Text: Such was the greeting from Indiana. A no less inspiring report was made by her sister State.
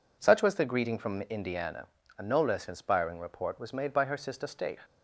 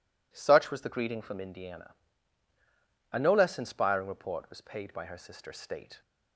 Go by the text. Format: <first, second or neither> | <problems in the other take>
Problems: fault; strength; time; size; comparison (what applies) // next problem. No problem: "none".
first | says "paid" for "made"; at 4.6 s